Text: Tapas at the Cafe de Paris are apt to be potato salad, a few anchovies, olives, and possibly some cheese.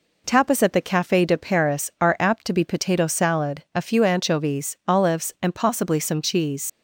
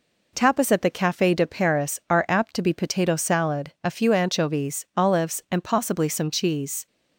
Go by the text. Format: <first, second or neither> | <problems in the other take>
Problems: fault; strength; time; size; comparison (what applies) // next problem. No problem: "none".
second | leaves "cheese" unfinished; at 6.6 s; 75 ms